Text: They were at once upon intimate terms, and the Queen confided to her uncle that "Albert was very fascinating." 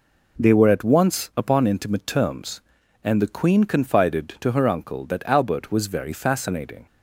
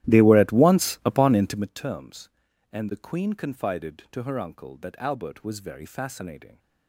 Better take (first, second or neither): first